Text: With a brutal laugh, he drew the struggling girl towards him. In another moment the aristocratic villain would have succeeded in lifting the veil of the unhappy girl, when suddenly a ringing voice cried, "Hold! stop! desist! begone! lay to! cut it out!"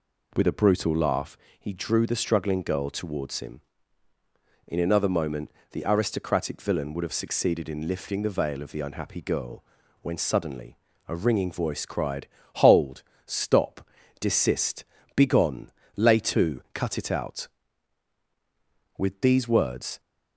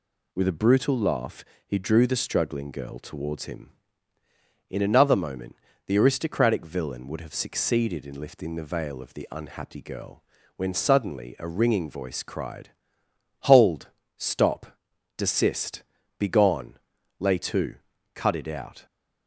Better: second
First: pauses between "moment" and "the"; slight; at 5.4 s; 0.22 s long // pauses between "suddenly" and "a"; slight; at 10.7 s; 0.30 s long // goes on to say "With these words"; noticeable; from 18.9 s on; 1.0 s long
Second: pauses between "moment" and "the"; slight; at 5.5 s; 0.32 s long

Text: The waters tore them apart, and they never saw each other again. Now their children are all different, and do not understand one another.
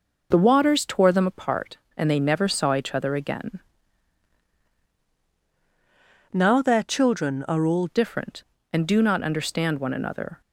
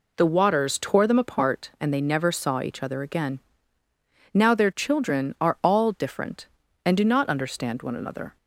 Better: second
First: changes voice from "Now" to "all"; from 6.3 to 7.8 s; 1.5 s long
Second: none

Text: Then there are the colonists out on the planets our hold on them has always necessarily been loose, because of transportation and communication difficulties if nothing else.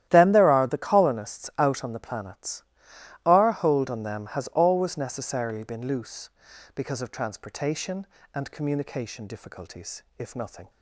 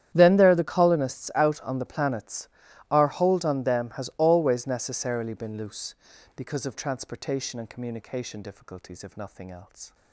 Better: second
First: starts louder than the rest; strong; until 1.1 s; 12 dB // pauses between "planets" and "our"; noticeable; at 2.6 s; 0.62 s long // pauses between "difficulties" and "if"; slight; at 10.0 s; 0.16 s long // stops before "else"; at 10.6 s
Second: starts louder than the rest; strong; until 1.1 s; 10 dB // pauses between "planets" and "our"; at 2.4 s; 0.42 s long

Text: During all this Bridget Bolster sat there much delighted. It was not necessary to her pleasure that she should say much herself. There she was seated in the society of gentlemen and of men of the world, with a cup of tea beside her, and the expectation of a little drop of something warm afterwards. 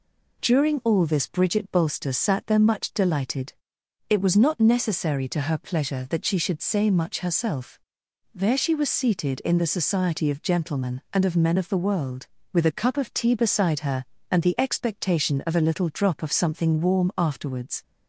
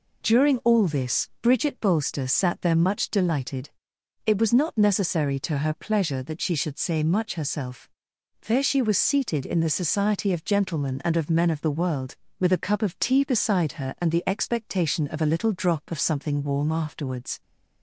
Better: neither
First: none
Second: none

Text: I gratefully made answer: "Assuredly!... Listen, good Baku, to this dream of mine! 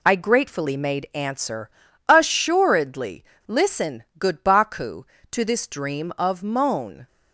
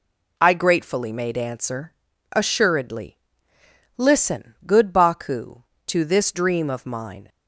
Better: second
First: says "moan" for "mine"; at 6.4 s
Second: none

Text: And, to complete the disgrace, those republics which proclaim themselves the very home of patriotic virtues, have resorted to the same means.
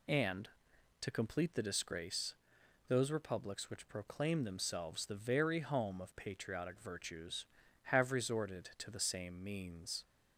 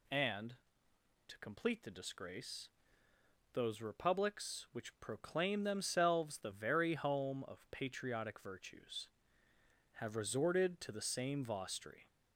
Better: first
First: none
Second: says "vostri" for "means"; at 11.4 s

